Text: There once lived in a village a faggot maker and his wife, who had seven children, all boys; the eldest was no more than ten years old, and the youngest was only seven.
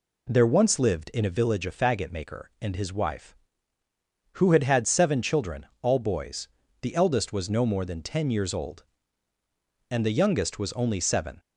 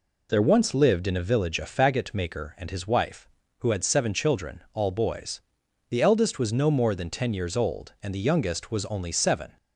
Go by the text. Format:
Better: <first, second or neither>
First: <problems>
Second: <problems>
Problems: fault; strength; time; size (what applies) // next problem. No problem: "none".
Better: second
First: says "had" twice; at 4.6 s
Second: none